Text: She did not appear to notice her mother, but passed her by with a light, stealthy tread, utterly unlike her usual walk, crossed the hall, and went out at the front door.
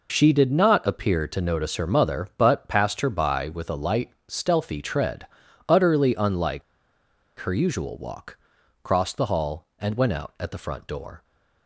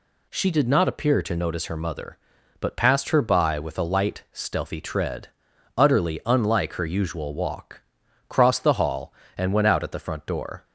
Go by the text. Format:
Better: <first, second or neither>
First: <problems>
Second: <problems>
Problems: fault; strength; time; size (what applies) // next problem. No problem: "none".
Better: second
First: pauses between "unlike" and "her"; noticeable; at 6.6 s; 0.77 s long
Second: none